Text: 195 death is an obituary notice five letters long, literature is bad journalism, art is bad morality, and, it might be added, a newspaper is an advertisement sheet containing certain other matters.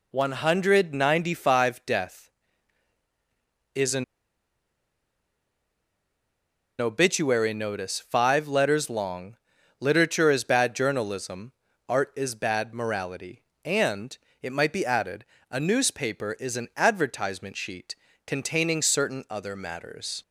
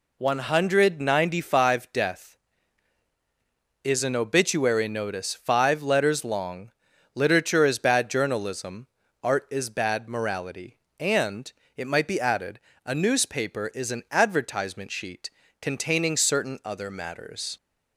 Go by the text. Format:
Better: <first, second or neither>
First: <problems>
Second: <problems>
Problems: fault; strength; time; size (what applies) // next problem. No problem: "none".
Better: second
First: pauses between "an" and "obituary"; strong; at 4.0 s; 2.7 s long // pauses between "sheet" and "containing"; slight; at 17.9 s; 0.32 s long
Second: pauses between "sheet" and "containing"; slight; at 15.3 s; 0.32 s long